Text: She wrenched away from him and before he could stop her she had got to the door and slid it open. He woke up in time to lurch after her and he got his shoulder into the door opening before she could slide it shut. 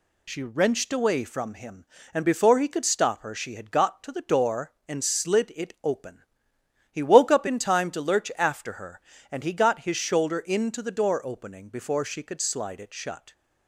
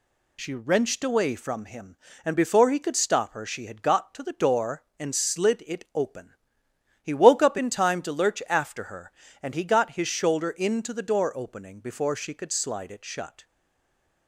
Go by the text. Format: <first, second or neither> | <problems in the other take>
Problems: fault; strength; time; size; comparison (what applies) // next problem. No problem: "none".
first | stays silent after the last word; slight; from 13.4 s on; 0.8 s long